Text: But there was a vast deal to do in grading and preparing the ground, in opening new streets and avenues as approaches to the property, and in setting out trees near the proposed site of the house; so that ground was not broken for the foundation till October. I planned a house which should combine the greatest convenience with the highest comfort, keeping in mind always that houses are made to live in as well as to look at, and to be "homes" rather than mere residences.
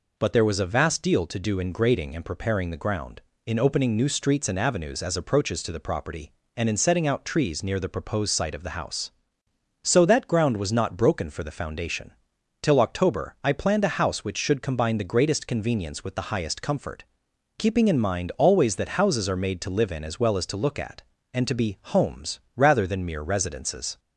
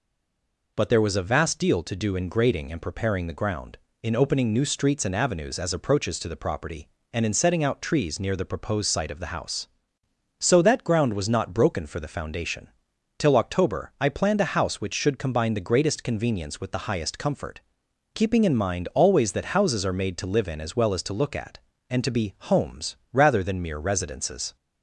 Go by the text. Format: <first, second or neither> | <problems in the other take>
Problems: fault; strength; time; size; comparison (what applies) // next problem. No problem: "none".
first | stays silent before the first word; slight; until 0.7 s; 0.7 s long // pauses between "foundation" and "till"; noticeable; at 12.6 s; 0.50 s long; noticeable in the first // pauses between "be" and "homes"; slight; at 22.3 s; 0.16 s long; slight in the first // pauses between "homes" and "rather"; slight; at 22.9 s; 0.16 s long; slight in the first